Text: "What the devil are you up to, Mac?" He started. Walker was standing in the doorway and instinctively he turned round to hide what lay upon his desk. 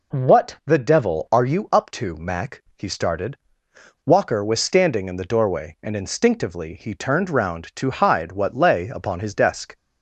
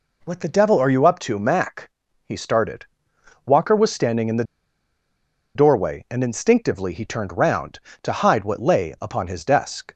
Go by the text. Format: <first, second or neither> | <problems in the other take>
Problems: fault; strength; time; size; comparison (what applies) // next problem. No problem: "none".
first | pauses between "the" and "doorway"; at 4.4 s; 1.1 s long